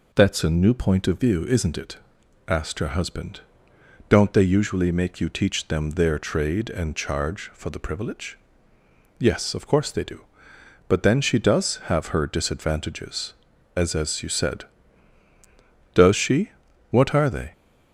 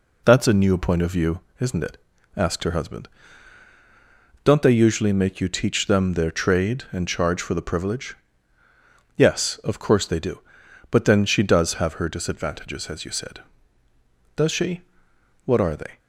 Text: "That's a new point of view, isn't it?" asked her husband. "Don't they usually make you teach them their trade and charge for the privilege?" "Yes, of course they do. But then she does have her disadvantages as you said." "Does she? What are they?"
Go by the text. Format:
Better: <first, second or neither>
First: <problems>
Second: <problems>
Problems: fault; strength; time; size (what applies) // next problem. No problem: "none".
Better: second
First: says "as" twice; at 13.9 s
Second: none